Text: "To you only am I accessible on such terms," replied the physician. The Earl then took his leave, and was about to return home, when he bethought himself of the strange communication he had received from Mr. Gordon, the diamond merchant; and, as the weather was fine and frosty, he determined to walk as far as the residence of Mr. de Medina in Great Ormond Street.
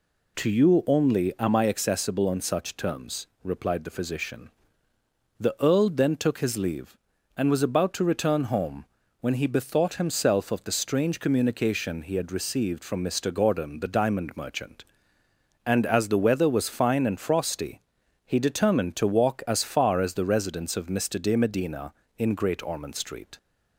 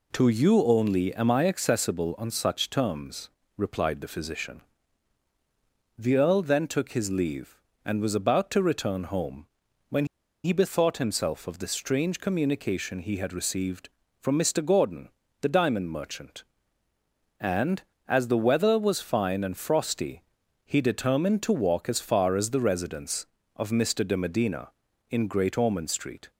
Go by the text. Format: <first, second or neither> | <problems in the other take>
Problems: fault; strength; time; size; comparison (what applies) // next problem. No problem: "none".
first | pauses between "when" and "he"; at 10.0 s; 0.38 s long